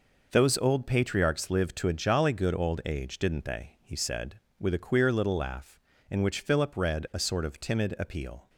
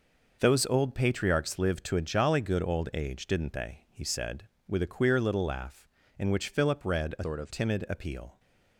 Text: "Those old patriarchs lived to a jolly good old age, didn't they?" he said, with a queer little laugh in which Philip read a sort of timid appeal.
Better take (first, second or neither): first